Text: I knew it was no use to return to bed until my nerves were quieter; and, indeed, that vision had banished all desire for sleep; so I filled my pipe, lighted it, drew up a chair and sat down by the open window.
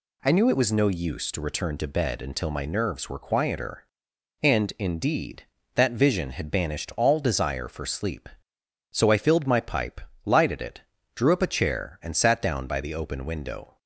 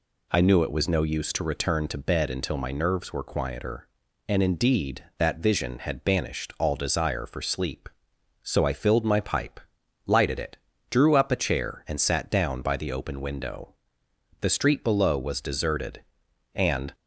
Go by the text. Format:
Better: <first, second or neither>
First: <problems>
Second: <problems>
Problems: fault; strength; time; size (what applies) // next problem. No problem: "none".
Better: first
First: none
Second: goes on to say "The street below was deserted and"; strong; from 14.4 s on; 2.5 s long